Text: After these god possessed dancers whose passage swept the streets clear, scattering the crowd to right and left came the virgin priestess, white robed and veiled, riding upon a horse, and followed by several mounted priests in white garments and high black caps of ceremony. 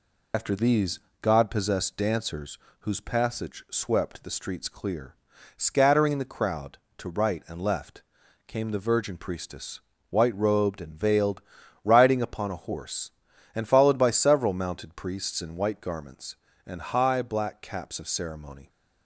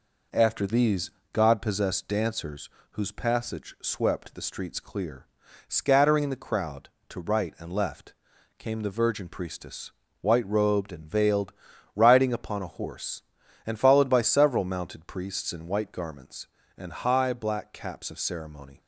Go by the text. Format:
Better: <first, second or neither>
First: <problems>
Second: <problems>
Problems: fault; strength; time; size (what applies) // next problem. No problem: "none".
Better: second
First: loses the start of "After"; at 0.3 s; 135 ms // pauses between "these" and "god"; slight; at 0.9 s; 0.22 s long // pauses between "dancers" and "whose"; slight; at 2.5 s; 0.22 s long // pauses between "left" and "came"; at 8.0 s; 0.44 s long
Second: pauses between "these" and "god"; slight; at 1.0 s; 0.22 s long // pauses between "dancers" and "whose"; slight; at 2.6 s; 0.22 s long // pauses between "left" and "came"; at 8.1 s; 0.44 s long